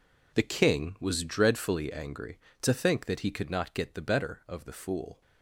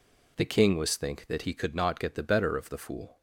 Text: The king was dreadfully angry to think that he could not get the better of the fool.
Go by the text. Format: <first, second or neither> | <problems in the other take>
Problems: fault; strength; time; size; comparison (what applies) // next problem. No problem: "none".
first | skips "dreadfully angry to"; at 0.9 s